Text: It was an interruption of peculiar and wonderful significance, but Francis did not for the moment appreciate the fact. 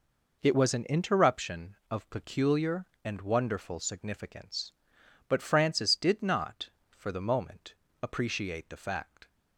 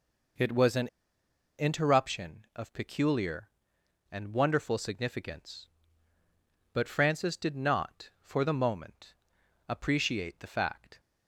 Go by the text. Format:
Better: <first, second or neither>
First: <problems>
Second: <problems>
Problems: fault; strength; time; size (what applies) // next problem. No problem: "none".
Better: first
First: pauses between "moment" and "appreciate"; slight; at 7.7 s; 0.28 s long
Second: pauses between "an" and "interruption"; noticeable; at 0.8 s; 0.72 s long // pauses between "moment" and "appreciate"; noticeable; at 9.1 s; 0.54 s long